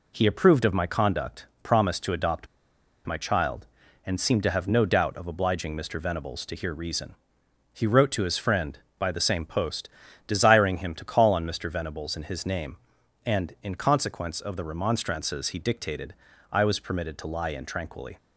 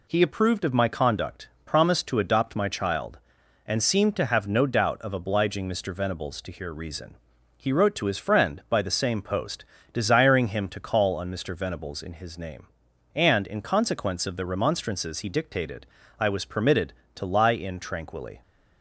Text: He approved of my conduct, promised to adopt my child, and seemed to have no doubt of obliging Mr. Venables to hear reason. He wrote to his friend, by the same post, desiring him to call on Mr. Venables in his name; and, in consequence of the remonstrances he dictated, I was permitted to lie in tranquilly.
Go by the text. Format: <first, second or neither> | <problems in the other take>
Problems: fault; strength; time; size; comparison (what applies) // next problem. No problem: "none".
second | pauses between "adopt" and "my"; noticeable; at 2.4 s; 0.60 s long